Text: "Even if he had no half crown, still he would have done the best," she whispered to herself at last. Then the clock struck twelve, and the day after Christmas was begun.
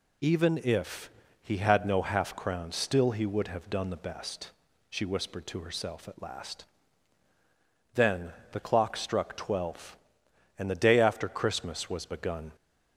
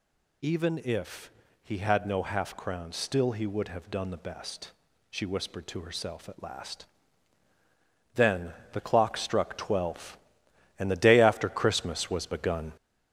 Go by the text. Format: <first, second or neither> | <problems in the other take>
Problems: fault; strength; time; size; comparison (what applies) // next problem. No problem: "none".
first | gets louder; noticeable; throughout; 4.5 dB // pauses between "if" and "he"; slight; at 1.2 s; 0.32 s long; slight in the first // pauses between "Then" and "the"; slight; at 8.5 s; 0.22 s long; slight in the first